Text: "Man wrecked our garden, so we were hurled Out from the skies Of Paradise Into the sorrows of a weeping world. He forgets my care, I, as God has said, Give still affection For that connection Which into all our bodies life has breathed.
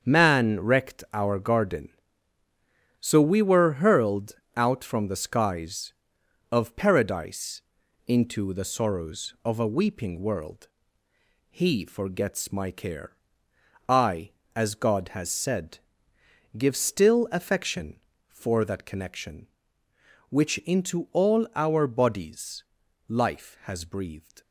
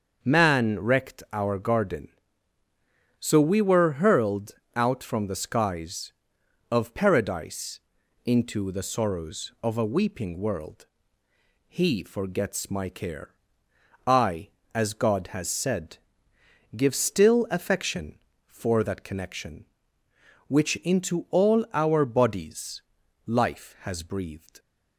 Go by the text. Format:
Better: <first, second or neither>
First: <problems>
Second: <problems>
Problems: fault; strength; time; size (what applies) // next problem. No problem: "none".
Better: second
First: gets quieter; strong; throughout; 8.5 dB // starts louder than the rest; strong; until 1.0 s; 7 dB // pauses between "hurled" and "Out"; slight; at 4.3 s; 0.24 s long // pauses between "Paradise" and "Into"; noticeable; at 7.6 s; 0.46 s long // pauses between "bodies" and "life"; at 22.6 s; 0.44 s long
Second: starts louder than the rest; until 1.2 s; 6.5 dB // pauses between "hurled" and "Out"; slight; at 4.5 s; 0.24 s long // pauses between "Paradise" and "Into"; noticeable; at 7.7 s; 0.46 s long // pauses between "bodies" and "life"; at 22.8 s; 0.44 s long